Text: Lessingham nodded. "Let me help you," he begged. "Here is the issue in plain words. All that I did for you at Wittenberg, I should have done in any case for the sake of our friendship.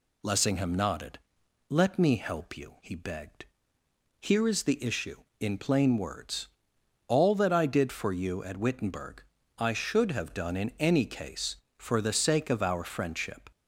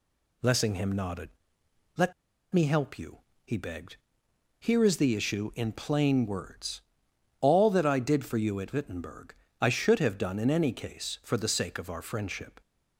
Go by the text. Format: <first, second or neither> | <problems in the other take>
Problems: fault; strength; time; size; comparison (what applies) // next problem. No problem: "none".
first | pauses between "Let" and "me"; at 2.1 s; 0.39 s long